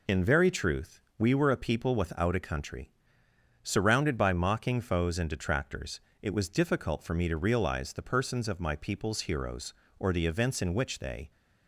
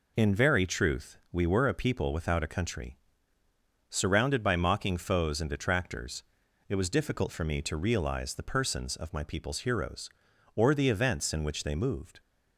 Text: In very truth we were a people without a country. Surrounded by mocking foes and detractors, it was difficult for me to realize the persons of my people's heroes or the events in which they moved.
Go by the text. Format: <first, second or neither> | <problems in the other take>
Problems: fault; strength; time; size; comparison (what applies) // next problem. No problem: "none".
second | pauses between "truth" and "we"; slight; at 1.0 s; 0.16 s long // stops before "moved"; at 11.3 s